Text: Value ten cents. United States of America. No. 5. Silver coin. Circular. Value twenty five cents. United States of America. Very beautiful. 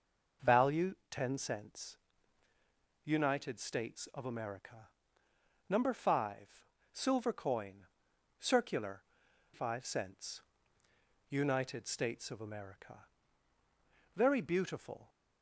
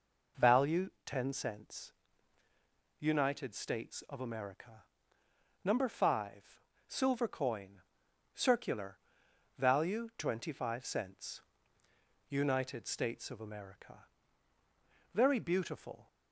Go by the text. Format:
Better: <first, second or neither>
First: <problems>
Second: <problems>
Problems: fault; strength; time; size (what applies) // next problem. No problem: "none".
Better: second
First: pauses between "Value" and "ten"; slight; at 0.9 s; 0.16 s long // skips "Value twenty"; at 9.2 s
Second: pauses between "Value" and "ten"; slight; at 0.8 s; 0.16 s long